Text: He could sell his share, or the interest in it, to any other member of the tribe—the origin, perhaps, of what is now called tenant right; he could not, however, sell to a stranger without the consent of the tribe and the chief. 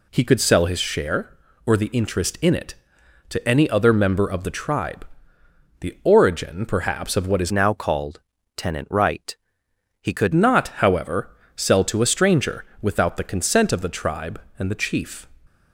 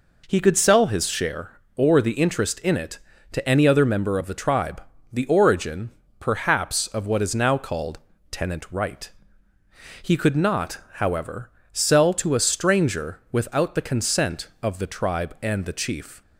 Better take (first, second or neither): second